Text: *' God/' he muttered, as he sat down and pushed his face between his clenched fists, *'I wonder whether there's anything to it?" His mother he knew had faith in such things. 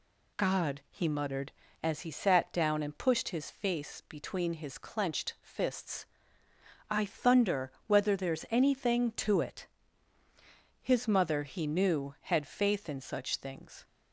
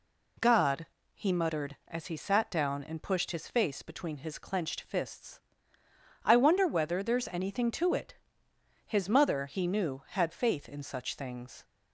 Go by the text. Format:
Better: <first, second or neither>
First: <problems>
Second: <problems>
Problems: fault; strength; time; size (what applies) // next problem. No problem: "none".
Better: second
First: says "thunder" for "wonder"; at 7.0 s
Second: none